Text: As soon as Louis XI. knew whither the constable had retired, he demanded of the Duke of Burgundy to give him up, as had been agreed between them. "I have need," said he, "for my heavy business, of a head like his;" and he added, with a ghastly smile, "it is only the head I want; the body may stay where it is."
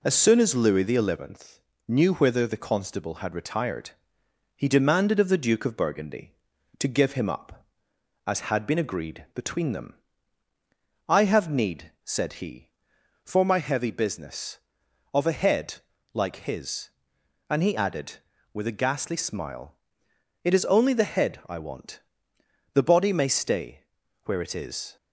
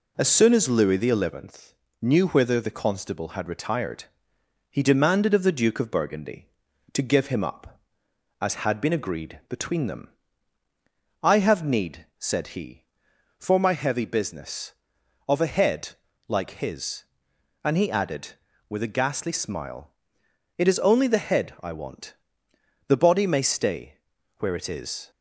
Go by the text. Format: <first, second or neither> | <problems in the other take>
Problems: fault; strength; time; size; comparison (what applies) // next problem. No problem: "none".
neither | pauses between "head" and "like"; the same in both // pauses between "stay" and "where"; the same in both